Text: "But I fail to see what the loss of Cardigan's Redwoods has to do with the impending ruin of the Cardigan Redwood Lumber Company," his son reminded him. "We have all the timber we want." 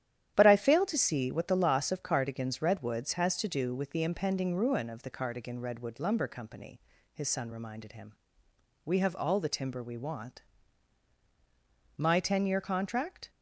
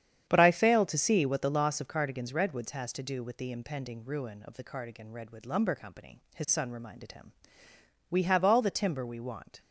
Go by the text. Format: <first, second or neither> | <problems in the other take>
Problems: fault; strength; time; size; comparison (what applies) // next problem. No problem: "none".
second | starts louder than the rest; strong; until 1.3 s; 11 dB; strong in the second // goes on to say "My ten year contract"; from 11.9 s on; 1.3 s long